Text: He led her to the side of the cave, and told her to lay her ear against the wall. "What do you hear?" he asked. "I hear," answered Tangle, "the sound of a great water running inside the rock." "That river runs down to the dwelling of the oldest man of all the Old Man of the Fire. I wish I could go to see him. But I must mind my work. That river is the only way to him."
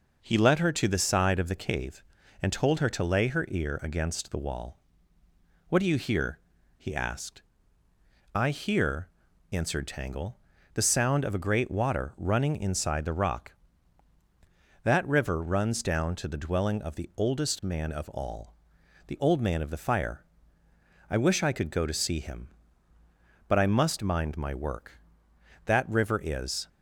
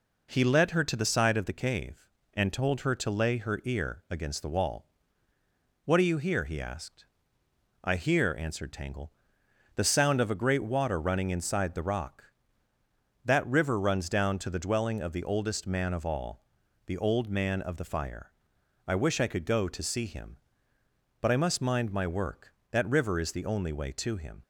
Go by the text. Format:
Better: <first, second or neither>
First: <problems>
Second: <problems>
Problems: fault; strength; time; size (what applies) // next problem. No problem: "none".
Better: second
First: pauses between "all" and "the"; noticeable; at 18.5 s; 0.52 s long // stops before "the only way to him"; at 26.6 s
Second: pauses between "all" and "the"; at 16.4 s; 0.40 s long